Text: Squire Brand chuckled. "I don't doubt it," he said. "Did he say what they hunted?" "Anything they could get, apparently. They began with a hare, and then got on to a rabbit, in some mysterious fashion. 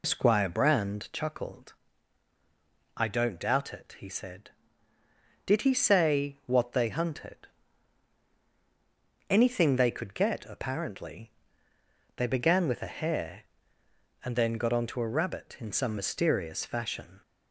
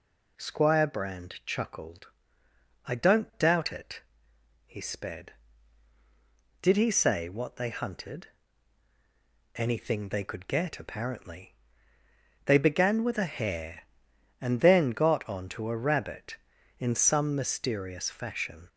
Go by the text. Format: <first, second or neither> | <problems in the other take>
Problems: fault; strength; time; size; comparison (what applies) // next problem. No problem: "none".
first | says "sped" for "said"; at 4.7 s